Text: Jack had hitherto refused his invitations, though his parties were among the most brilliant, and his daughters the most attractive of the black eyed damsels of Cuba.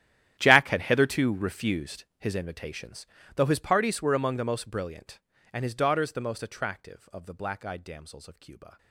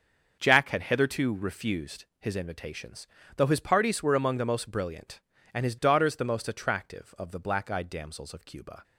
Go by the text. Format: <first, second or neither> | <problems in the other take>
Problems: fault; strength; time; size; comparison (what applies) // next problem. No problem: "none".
second | gets quieter; strong; throughout; 19 dB // starts louder than the rest; strong; until 1.4 s; 11.5 dB; also in the second